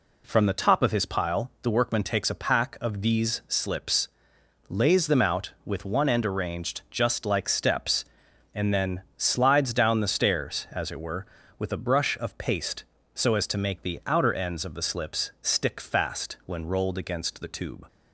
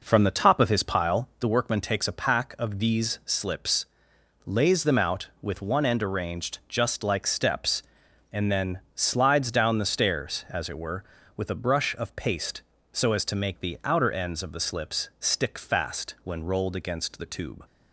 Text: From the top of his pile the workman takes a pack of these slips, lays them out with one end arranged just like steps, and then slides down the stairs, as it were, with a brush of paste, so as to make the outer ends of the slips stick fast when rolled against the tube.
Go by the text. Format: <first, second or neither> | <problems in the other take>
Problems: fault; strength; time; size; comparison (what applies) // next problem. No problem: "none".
first | starts louder than the rest; noticeable; until 1.5 s; 5 dB // pauses between "then" and "slides"; slight; at 8.7 s; 0.16 s long; slight in the first